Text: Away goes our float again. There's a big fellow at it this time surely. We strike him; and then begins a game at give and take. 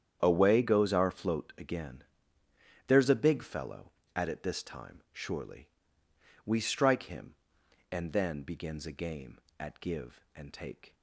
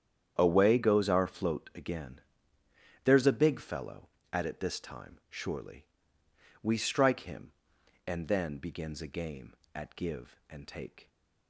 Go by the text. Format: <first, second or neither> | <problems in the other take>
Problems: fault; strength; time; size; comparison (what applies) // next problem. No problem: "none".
neither | starts louder than the rest; strong; the same in both